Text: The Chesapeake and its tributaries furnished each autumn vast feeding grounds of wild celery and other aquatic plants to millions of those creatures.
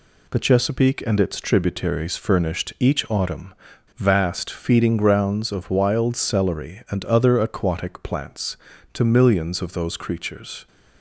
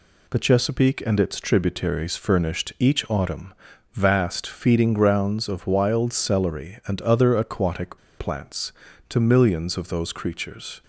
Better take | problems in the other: first | pauses between "autumn" and "vast"; at 3.5 s; 0.40 s long; also in the first // pauses between "aquatic" and "plants"; slight; at 7.9 s; 0.20 s long

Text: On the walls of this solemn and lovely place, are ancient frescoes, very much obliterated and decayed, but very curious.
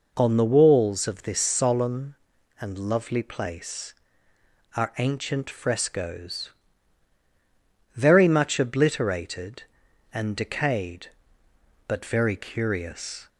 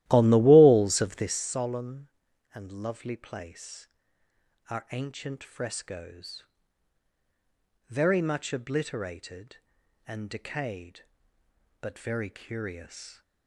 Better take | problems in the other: first | starts louder than the rest; strong; until 1.4 s; 14.5 dB

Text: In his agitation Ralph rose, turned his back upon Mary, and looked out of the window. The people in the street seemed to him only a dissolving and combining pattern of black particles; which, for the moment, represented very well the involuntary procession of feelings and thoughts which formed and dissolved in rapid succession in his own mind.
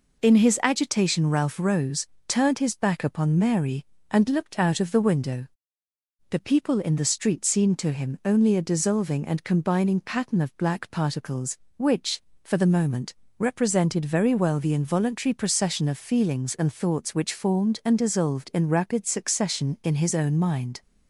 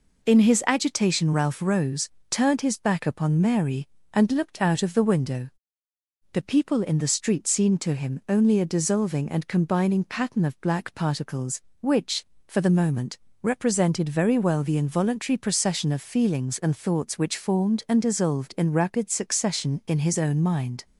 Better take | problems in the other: neither | none

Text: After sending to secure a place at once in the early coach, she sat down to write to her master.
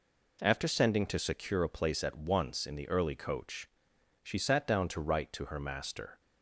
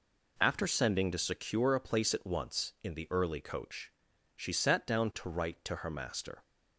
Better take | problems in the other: neither | none

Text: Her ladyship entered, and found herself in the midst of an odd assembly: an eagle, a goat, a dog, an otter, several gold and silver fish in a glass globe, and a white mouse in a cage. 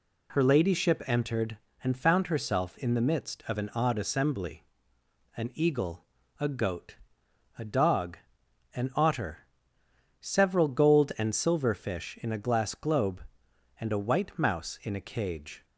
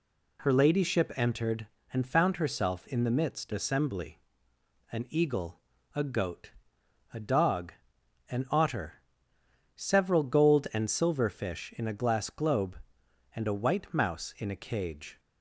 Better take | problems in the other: first | skips "of an odd"; at 3.5 s

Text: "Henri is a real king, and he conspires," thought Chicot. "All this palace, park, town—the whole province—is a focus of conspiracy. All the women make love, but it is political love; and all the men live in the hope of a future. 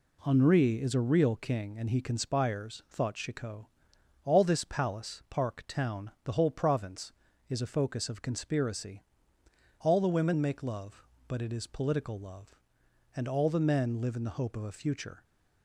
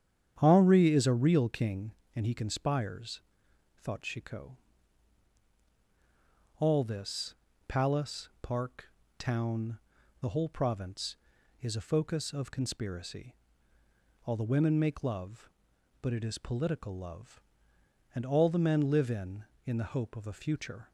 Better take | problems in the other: first | starts louder than the rest; strong; until 1.3 s; 9 dB // pauses between "this" and "palace"; slight; at 7.3 s; 0.34 s long // says "in" twice; at 19.6 s

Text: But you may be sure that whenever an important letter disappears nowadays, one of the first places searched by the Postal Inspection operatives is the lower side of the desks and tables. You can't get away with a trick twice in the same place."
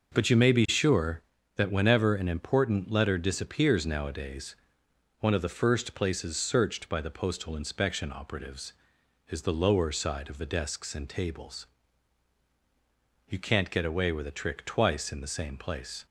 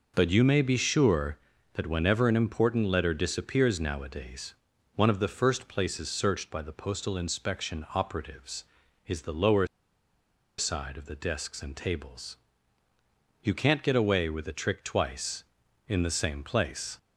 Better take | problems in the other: first | pauses between "lower" and "side"; noticeable; at 9.6 s; 0.91 s long

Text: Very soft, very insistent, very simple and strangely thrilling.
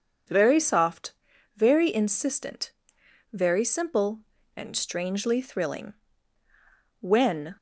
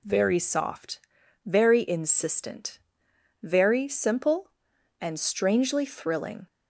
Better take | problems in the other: second | goes on to say "When"; from 7.0 s on; 0.56 s long

